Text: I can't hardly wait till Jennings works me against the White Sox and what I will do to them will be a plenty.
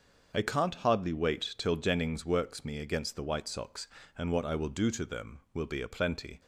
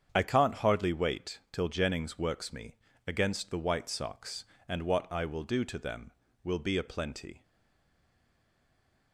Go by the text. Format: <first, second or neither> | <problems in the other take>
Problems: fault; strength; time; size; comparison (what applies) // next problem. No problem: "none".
first | starts louder than the rest; strong; until 1.1 s; 8 dB; also in the first // pauses between "me" and "against"; slight; at 2.7 s; 0.32 s long // stays silent after the last word; noticeable; from 7.4 s on; 1.7 s long